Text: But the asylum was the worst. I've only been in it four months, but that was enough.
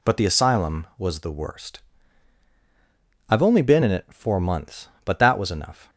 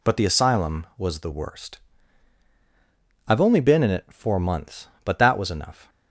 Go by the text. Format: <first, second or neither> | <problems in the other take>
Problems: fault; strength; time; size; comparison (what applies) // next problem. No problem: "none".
neither | none